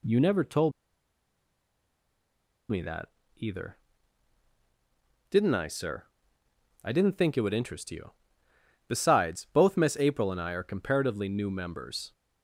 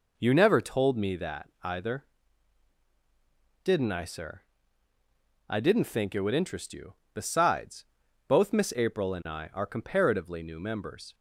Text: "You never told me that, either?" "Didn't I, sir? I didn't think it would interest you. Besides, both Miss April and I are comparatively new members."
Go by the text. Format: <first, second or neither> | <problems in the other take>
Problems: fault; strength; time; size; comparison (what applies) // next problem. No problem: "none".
second | pauses between "told" and "me"; strong; at 0.7 s; 2.0 s long